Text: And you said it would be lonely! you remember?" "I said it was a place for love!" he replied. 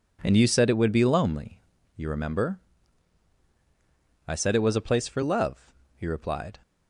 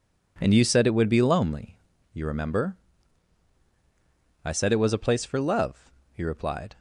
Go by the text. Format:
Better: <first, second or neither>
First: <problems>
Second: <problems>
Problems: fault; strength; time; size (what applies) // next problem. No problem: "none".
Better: neither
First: none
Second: none